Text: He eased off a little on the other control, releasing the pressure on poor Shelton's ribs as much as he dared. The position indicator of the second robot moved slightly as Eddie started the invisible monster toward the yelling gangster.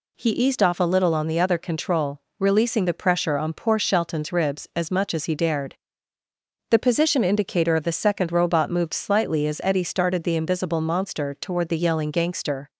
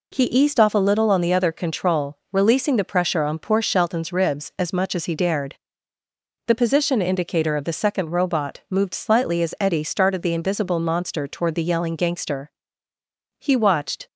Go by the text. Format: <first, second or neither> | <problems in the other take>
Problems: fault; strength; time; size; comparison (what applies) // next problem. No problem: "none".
first | goes on to say "He watched"; noticeable; from 13.3 s on; 0.68 s long